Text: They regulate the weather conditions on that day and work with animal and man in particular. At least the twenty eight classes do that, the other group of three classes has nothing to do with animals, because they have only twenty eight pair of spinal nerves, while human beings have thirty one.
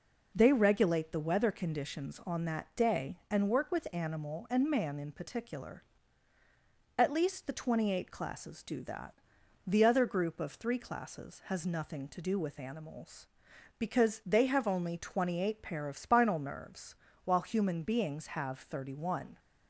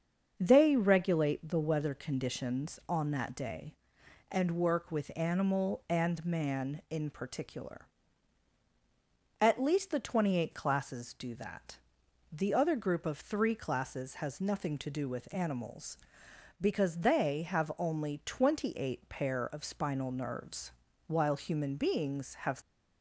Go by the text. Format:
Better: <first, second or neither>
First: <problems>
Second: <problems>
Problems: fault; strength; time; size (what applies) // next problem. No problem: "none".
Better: first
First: none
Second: starts louder than the rest; until 1.3 s; 6.5 dB // stops before "thirty one"; at 22.6 s